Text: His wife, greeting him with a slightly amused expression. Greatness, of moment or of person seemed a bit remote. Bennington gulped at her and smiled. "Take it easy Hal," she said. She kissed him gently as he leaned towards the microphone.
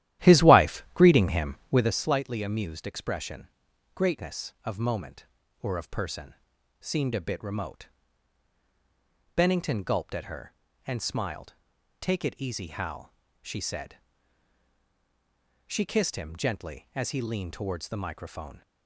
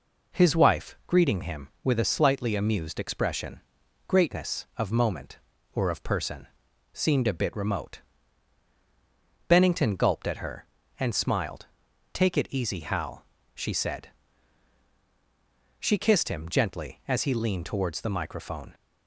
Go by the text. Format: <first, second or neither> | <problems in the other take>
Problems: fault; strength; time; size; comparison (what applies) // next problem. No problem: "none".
second | starts louder than the rest; strong; until 2.0 s; 13 dB // pauses between "person" and "seemed"; noticeable; at 6.3 s; 0.48 s long; noticeable in the second